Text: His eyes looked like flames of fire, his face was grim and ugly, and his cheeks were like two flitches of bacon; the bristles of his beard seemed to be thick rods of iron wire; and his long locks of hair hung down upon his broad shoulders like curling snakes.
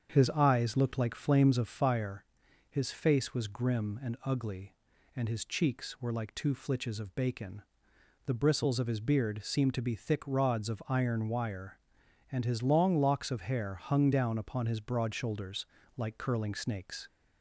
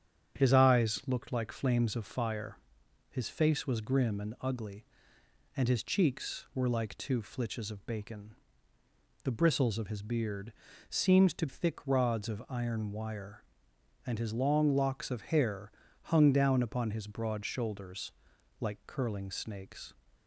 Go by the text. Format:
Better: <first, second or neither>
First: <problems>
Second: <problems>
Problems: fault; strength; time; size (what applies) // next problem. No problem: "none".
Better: first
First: starts louder than the rest; strong; until 1.1 s; 7.5 dB // pauses between "shoulders" and "like"; slight; at 15.6 s; 0.28 s long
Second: starts louder than the rest; strong; until 1.4 s; 8.5 dB // pauses between "beard" and "seemed"; at 10.5 s; 0.38 s long // skips "be"; at 11.4 s // pauses between "hair" and "hung"; slight; at 15.7 s; 0.30 s long // pauses between "shoulders" and "like"; noticeable; at 18.1 s; 0.48 s long